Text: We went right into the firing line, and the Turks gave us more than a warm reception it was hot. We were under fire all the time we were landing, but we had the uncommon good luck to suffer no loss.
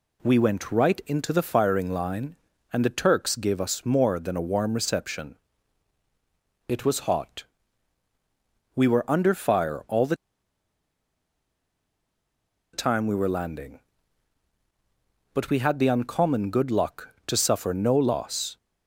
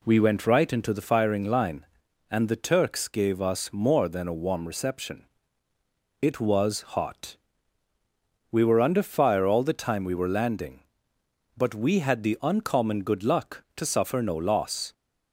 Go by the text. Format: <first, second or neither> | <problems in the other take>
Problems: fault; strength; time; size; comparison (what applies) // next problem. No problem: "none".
second | pauses between "reception" and "it"; strong; at 5.3 s; 1.3 s long; noticeable in the second // pauses between "the" and "time"; strong; at 10.1 s; 2.5 s long